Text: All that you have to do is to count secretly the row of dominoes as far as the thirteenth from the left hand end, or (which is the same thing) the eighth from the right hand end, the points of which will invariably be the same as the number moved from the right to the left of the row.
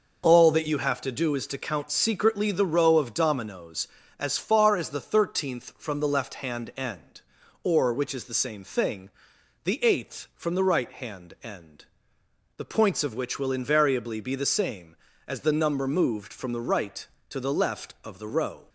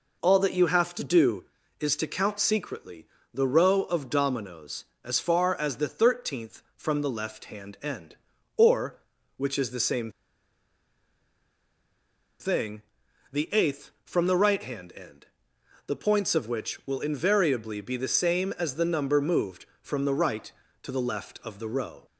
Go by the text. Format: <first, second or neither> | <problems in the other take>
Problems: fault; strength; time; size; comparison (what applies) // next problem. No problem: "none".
first | pauses between "secretly" and "the"; slight; at 3.0 s; 0.26 s long // pauses between "same" and "thing"; strong; at 10.0 s; 2.3 s long